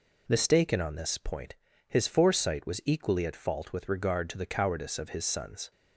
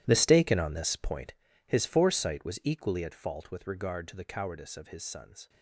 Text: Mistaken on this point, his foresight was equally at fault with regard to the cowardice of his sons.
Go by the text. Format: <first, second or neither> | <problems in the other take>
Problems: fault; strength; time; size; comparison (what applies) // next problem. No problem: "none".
first | gets quieter; strong; throughout; 15.5 dB